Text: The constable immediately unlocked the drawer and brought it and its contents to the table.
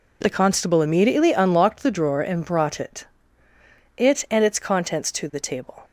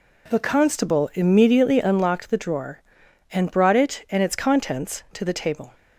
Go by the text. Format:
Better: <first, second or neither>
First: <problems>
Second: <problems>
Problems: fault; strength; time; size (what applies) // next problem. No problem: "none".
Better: second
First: says "it" twice; at 3.9 s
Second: none